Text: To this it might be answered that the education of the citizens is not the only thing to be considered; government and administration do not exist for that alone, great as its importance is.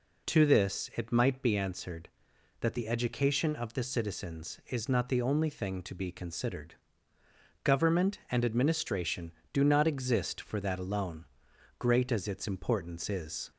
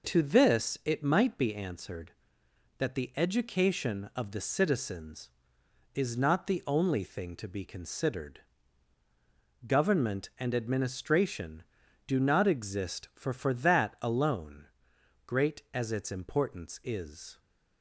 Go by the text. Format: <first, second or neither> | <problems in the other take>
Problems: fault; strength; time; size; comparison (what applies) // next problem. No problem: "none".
first | says "for" twice; at 13.3 s